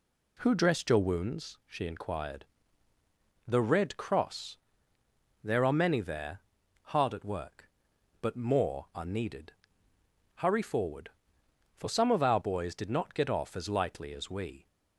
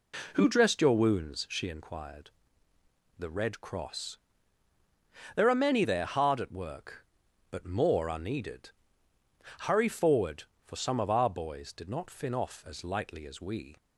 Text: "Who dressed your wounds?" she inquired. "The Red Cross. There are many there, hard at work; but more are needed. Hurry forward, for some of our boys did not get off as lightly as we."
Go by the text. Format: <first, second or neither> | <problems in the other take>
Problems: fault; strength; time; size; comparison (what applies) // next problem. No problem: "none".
first | says "fin" for "get"; at 12.1 s